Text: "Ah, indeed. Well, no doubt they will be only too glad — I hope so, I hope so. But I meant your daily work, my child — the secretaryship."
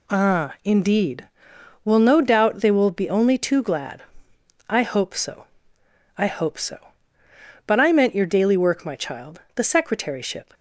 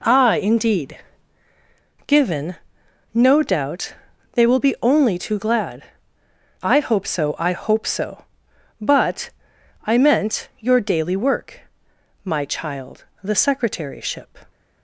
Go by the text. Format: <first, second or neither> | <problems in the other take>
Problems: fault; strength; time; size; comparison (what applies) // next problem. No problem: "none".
first | says "Given" for "Well"; at 2.0 s // pauses between "doubt" and "they"; at 3.9 s; 0.38 s long // pauses between "But" and "I"; noticeable; at 9.2 s; 0.56 s long